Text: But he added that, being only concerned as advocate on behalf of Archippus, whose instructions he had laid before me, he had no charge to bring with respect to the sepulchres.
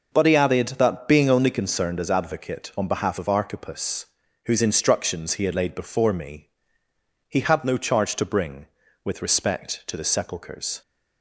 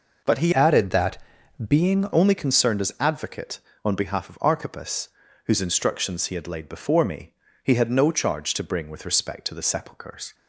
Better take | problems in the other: first | changes voice from "added" to "being"; from 0.5 to 2.0 s; 1.5 s long

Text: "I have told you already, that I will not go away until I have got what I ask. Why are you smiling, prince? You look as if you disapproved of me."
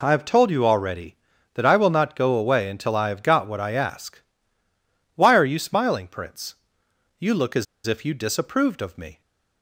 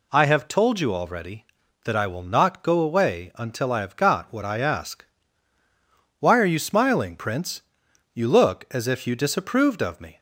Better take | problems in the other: second | pauses between "as" and "if"; slight; at 7.6 s; 0.21 s long

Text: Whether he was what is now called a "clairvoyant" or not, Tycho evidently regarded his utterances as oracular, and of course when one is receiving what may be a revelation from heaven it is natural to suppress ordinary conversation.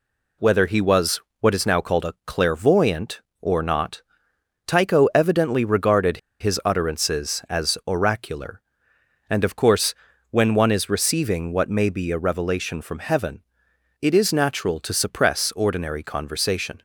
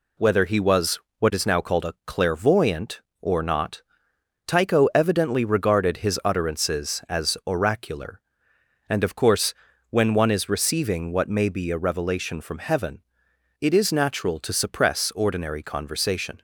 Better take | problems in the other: second | pauses between "was" and "what"; slight; at 1.1 s; 0.22 s long; slight in the second // pauses between "regarded" and "his"; slight; at 6.1 s; 0.23 s long // pauses between "course" and "when"; at 9.9 s; 0.38 s long; also in the second // pauses between "heaven" and "it"; noticeable; at 13.4 s; 0.60 s long; noticeable in the second

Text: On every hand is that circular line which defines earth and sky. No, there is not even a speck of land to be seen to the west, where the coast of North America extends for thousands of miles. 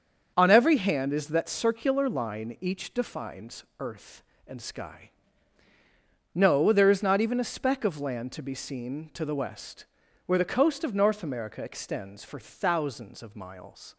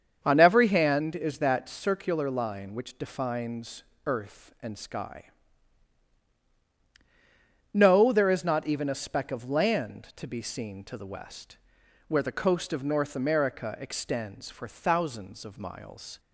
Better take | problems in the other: second | starts louder than the rest; until 1.3 s; 7 dB; strong in the second // says "each" for "which"; at 2.5 s // pauses between "defines" and "earth"; slight; at 3.6 s; 0.16 s long; slight in the second

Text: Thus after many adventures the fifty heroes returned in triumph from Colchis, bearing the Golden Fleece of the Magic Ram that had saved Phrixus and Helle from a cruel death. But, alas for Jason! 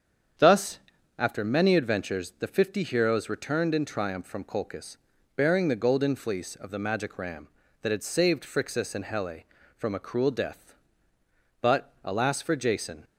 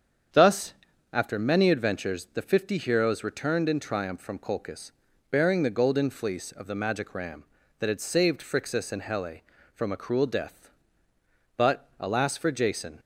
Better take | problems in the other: neither | starts louder than the rest; strong; the same in both // pauses between "Thus" and "after"; the same in both

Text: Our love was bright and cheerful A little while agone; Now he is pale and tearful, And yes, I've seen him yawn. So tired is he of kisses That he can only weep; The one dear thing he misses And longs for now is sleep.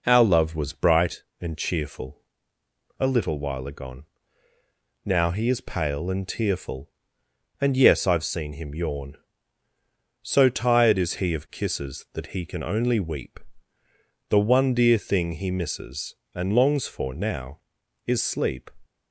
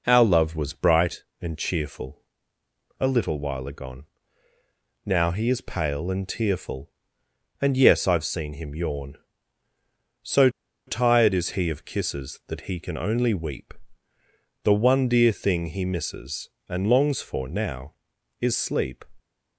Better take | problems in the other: first | pauses between "cheerful" and "A"; noticeable; at 2.2 s; 0.76 s long; noticeable in the first // pauses between "So" and "tired"; at 10.4 s; 0.38 s long

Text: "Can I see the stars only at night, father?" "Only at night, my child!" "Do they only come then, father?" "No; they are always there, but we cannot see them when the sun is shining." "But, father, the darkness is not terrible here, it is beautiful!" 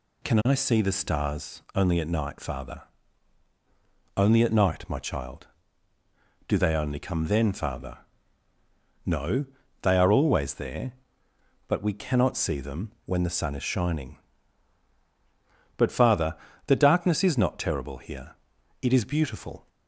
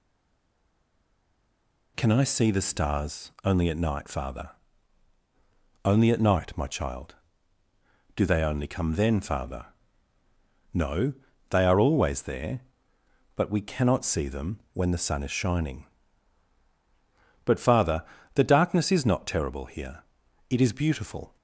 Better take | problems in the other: first | stays silent before the first word; noticeable; until 1.9 s; 1.9 s long

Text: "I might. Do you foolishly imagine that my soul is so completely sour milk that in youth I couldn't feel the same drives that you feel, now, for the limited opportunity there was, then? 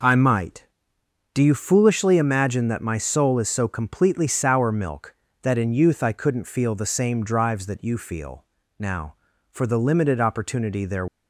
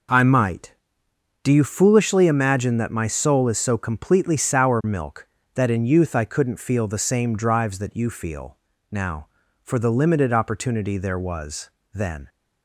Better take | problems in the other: second | stops before "was then"; at 11.0 s

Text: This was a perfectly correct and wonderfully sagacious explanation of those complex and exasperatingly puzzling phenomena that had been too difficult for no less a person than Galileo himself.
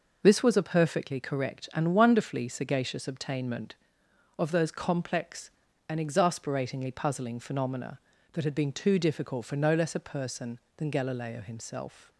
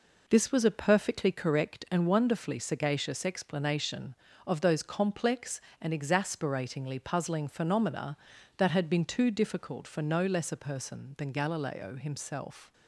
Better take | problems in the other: second | says "obtainment" for "explanation"; at 3.0 s

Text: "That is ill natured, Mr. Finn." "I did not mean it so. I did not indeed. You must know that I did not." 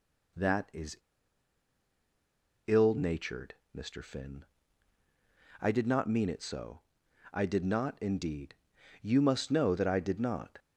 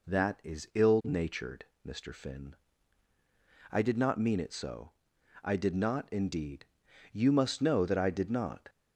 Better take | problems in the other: second | pauses between "is" and "ill"; strong; at 0.9 s; 1.6 s long

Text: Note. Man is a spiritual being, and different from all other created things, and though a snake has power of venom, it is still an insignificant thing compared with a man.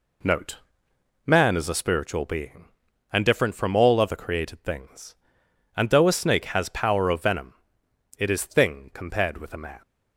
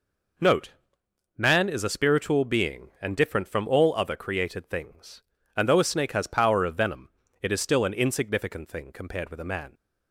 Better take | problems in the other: second | skips "still an insignificant"; at 8.4 s

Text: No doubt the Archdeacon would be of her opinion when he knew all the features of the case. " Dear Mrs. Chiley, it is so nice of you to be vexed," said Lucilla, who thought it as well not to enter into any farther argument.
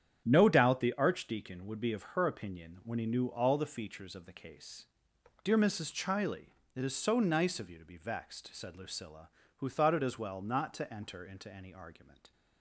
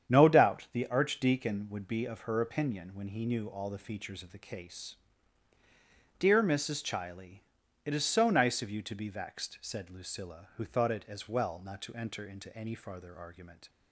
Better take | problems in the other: second | starts louder than the rest; strong; until 1.2 s; 9 dB; strong in the second // skips "farther"; at 11.7 s

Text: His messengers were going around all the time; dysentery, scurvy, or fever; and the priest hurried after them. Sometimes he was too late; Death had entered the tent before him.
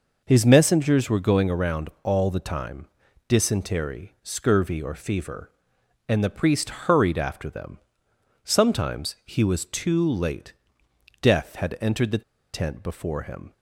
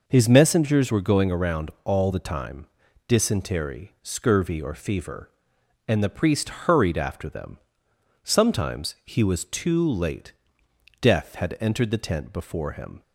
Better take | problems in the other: second | pauses between "priest" and "hurried"; slight; at 6.6 s; 0.18 s long; slight in the second // pauses between "the" and "tent"; slight; at 12.2 s; 0.30 s long

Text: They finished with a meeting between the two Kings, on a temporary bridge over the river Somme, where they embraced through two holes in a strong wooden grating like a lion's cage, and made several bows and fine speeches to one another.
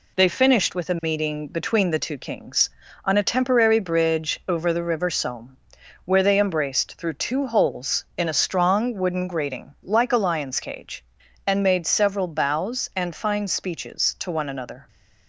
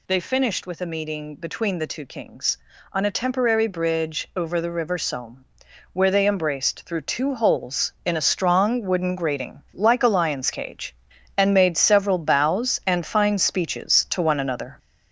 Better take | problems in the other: first | gets louder; noticeable; throughout; 5.5 dB

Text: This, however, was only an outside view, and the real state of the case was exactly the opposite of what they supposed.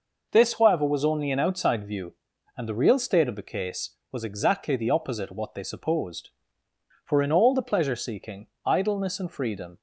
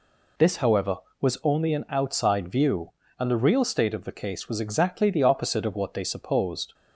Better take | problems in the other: second | goes on to say "For in all the pleasure seeking idleness and freedom"; strong; from 7.0 s on; 2.7 s long

